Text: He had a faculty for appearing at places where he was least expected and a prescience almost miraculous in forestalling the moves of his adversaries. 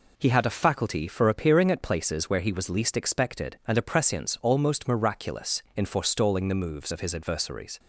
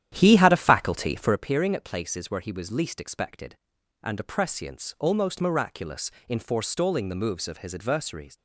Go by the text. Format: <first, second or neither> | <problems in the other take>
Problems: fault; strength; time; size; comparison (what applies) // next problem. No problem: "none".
first | starts louder than the rest; strong; until 1.4 s; 10.5 dB